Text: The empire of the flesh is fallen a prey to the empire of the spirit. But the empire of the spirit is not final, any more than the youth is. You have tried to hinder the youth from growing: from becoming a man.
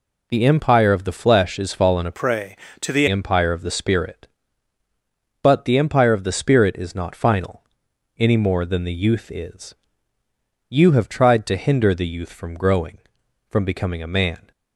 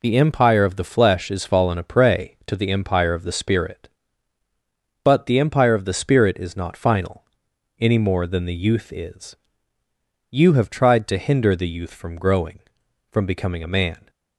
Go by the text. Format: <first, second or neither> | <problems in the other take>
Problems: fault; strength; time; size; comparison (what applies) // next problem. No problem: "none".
second | changes voice from "prey" to "the"; from 2.1 to 3.0 s; 0.9 s long